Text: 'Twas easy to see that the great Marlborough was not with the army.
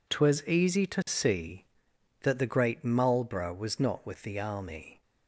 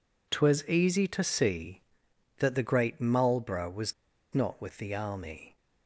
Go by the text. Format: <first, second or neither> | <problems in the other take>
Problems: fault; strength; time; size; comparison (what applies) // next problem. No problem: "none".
first | pauses between "was" and "not"; at 3.9 s; 0.41 s long